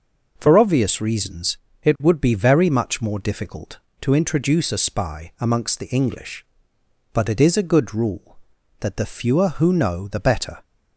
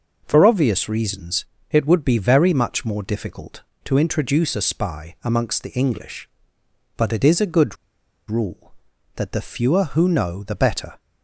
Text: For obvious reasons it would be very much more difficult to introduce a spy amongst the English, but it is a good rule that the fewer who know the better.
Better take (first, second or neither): first